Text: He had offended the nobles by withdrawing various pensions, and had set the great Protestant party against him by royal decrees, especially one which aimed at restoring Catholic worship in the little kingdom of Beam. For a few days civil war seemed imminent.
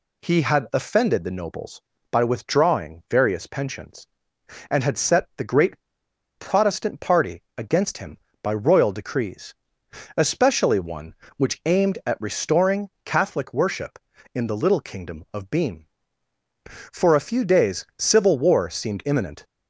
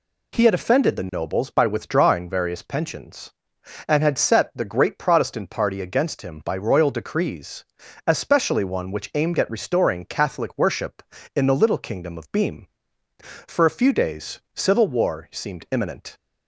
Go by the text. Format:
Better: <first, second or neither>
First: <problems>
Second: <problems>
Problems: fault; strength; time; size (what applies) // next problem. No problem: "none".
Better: second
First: pauses between "great" and "Protestant"; noticeable; at 5.8 s; 0.55 s long // pauses between "party" and "against"; slight; at 7.4 s; 0.16 s long // pauses between "restoring" and "Catholic"; slight; at 12.8 s; 0.16 s long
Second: none